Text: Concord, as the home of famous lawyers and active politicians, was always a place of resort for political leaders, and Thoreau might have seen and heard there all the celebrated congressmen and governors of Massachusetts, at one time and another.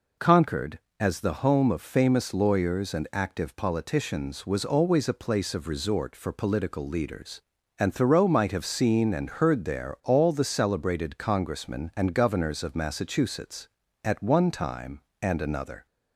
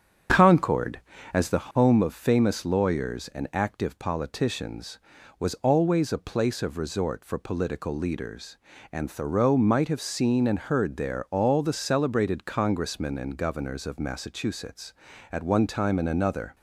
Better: first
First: none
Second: starts louder than the rest; strong; until 1.7 s; 8 dB

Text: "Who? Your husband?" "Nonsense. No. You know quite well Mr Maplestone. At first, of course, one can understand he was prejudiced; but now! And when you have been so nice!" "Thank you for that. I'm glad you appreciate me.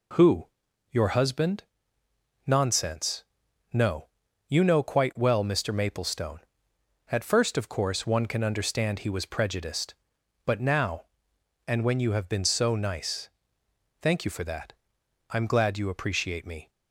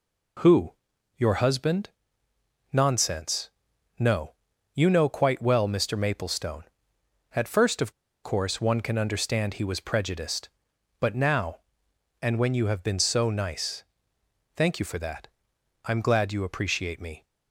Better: first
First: none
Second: pauses between "of" and "course"; slight; at 7.9 s; 0.31 s long

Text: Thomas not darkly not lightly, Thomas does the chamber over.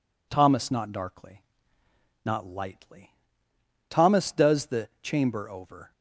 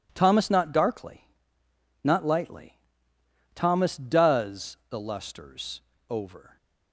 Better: first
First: pauses between "darkly" and "not"; noticeable; at 1.4 s; 0.84 s long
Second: pauses between "darkly" and "not"; noticeable; at 1.2 s; 0.76 s long // says "lusters" for "chamber"; at 4.9 s

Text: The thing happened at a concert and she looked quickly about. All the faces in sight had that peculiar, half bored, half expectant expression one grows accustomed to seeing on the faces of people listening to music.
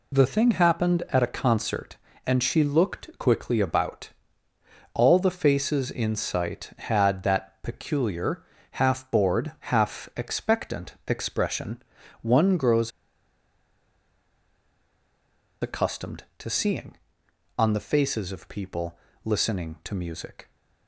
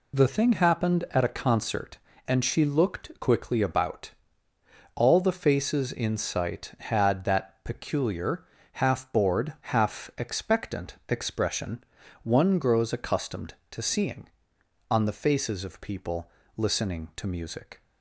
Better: second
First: pauses between "expression" and "one"; at 11.8 s; 0.40 s long // pauses between "grows" and "accustomed"; strong; at 12.9 s; 2.7 s long // pauses between "people" and "listening"; slight; at 18.9 s; 0.26 s long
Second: pauses between "expression" and "one"; at 11.8 s; 0.40 s long // pauses between "people" and "listening"; slight; at 16.3 s; 0.26 s long

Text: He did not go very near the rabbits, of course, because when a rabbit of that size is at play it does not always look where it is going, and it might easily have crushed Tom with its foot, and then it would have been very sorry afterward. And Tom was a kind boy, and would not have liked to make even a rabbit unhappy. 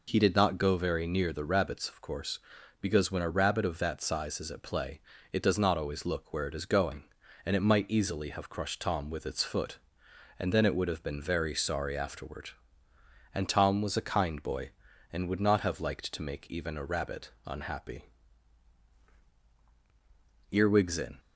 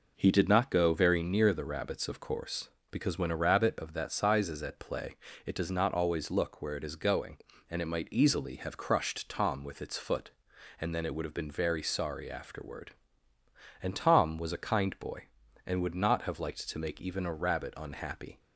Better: second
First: pauses between "play" and "it"; slight; at 5.0 s; 0.32 s long // pauses between "rabbit" and "unhappy"; slight; at 17.2 s; 0.16 s long // goes on to say "Earwigs in"; noticeable; from 20.5 s on; 0.68 s long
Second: pauses between "play" and "it"; slight; at 5.1 s; 0.30 s long

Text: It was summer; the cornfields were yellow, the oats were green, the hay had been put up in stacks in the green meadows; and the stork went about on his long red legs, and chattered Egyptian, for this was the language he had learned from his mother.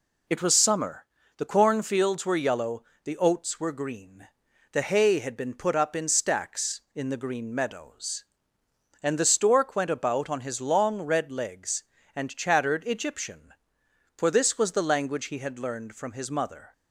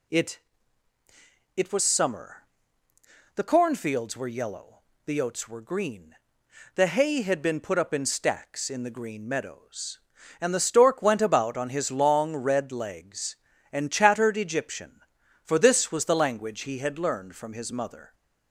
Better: first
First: none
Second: says "It" twice; at 1.5 s

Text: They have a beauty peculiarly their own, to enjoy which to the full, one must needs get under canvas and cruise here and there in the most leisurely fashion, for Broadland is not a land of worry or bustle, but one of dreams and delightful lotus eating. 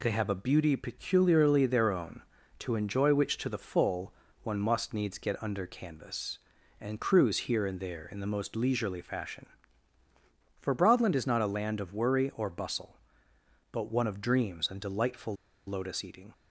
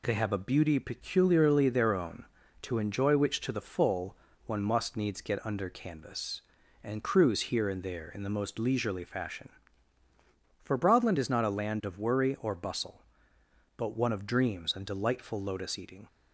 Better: second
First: pauses between "delightful" and "lotus"; slight; at 15.3 s; 0.32 s long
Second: none

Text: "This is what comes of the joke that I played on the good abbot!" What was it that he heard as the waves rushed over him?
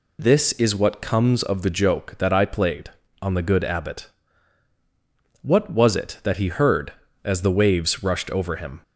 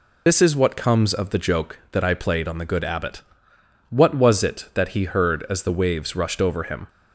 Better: first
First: none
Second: loses the start of "This"; at 0.2 s; 85 ms

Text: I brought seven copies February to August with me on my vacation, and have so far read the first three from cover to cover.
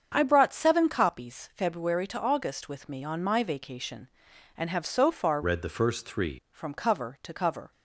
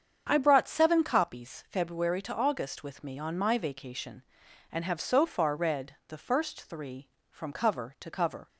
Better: second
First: starts louder than the rest; strong; until 1.1 s; 7 dB // changes voice from "read" to "three"; from 5.4 to 6.3 s; 0.9 s long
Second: starts louder than the rest; strong; until 1.3 s; 7.5 dB

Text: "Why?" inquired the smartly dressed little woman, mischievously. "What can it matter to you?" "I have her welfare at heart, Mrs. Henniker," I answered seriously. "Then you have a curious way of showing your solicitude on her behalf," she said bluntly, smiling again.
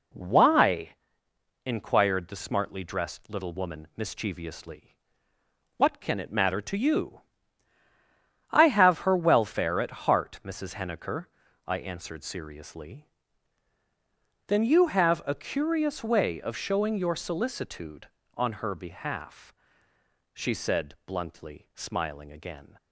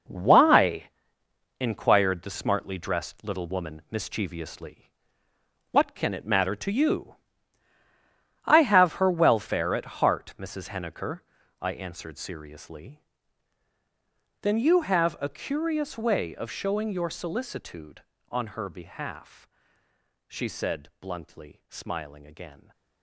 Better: first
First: none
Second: gets quieter; strong; throughout; 9.5 dB

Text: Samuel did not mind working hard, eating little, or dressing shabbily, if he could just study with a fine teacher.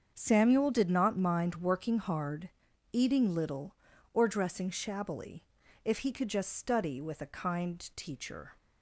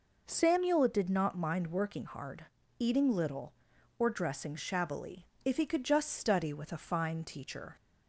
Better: second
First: starts louder than the rest; strong; until 1.1 s; 7 dB // says "kind" for "fine"; at 7.3 s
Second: none

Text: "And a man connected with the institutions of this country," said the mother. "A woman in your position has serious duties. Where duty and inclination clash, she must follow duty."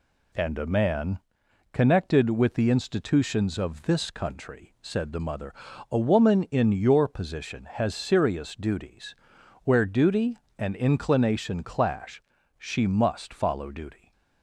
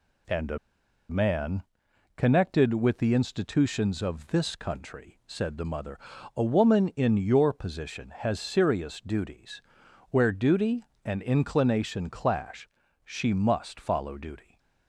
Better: first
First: pauses between "man" and "connected"; noticeable; at 1.1 s; 0.54 s long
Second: pauses between "a" and "man"; noticeable; at 0.5 s; 0.52 s long // pauses between "man" and "connected"; noticeable; at 1.6 s; 0.54 s long

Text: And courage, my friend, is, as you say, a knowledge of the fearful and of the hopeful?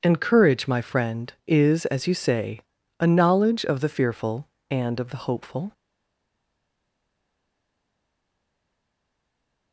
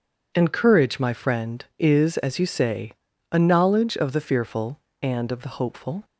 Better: second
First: stays silent after the last word; strong; from 5.7 s on; 4.0 s long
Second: none

